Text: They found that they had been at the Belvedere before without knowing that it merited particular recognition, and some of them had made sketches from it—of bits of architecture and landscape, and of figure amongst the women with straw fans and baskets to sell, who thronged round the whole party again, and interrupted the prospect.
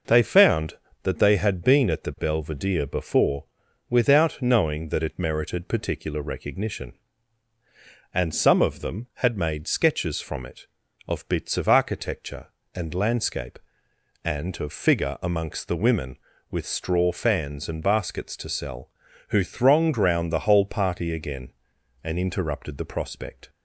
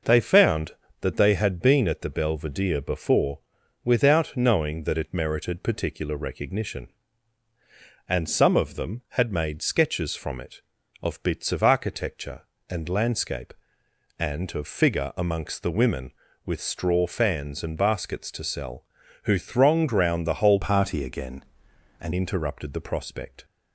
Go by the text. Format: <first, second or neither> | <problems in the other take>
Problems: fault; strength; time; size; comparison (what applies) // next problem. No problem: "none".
first | pauses between "before" and "without"; at 3.3 s; 0.44 s long; also in the first // changes voice from "party" to "and"; from 20.6 to 22.1 s; 1.5 s long